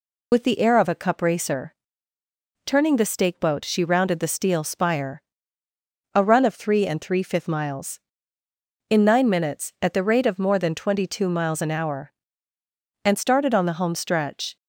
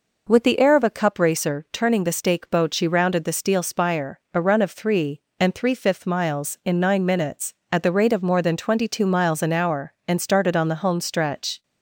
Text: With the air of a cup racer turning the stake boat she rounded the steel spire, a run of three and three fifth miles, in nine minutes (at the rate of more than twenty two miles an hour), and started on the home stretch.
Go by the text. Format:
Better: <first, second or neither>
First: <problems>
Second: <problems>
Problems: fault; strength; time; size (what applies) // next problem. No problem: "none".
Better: second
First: loses the start of "With"; at 0.3 s; 50 ms // pauses between "racer" and "turning"; noticeable; at 1.7 s; 0.90 s long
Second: none